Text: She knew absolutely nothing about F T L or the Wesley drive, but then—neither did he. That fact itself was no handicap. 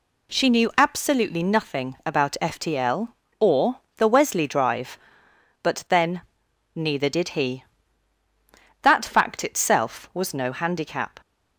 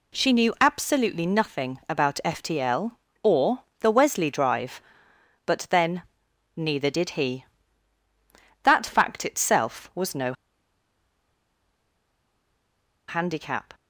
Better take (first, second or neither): first